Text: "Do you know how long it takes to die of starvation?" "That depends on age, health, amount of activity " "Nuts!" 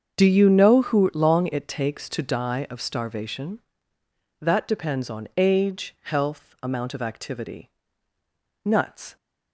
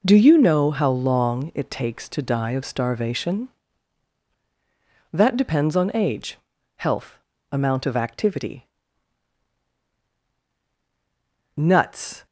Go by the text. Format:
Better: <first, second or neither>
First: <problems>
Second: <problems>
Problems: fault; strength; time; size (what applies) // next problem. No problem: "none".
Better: second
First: starts louder than the rest; strong; until 1.2 s; 7.5 dB // says "who" for "how"; at 0.8 s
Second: starts louder than the rest; until 1.0 s; 6.5 dB